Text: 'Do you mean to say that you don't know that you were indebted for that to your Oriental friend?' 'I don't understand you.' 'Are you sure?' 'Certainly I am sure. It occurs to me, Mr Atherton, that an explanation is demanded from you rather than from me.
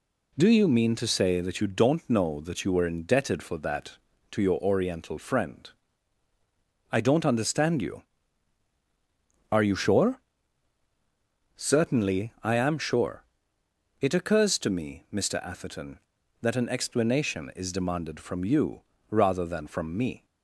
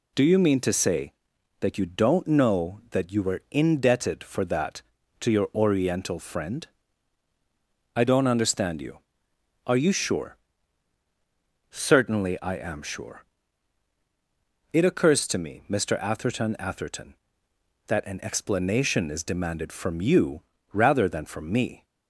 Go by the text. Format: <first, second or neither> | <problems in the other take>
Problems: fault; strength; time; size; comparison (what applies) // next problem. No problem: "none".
first | says "Atherton" twice; at 16.5 s // pauses between "you" and "rather"; slight; at 20.4 s; 0.28 s long; slight in the first